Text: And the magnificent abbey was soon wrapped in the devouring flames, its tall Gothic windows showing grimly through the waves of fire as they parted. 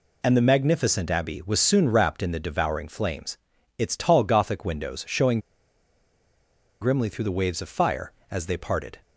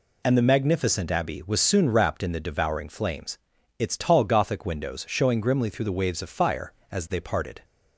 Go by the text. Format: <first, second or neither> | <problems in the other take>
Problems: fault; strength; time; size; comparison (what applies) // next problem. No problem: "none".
second | pauses between "showing" and "grimly"; strong; at 5.3 s; 1.4 s long